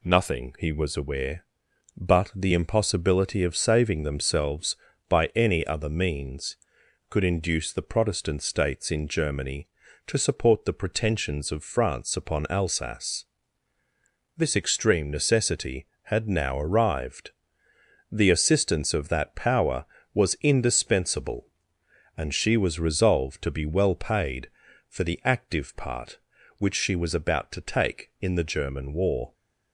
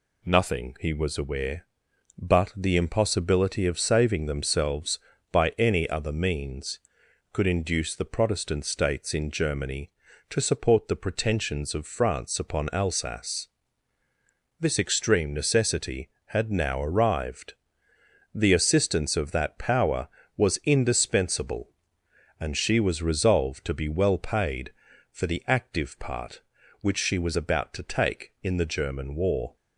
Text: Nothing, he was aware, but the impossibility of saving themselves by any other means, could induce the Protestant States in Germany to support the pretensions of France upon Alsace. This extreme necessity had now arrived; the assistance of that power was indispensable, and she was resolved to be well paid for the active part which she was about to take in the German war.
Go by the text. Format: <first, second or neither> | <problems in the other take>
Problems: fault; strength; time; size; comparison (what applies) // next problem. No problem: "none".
neither | none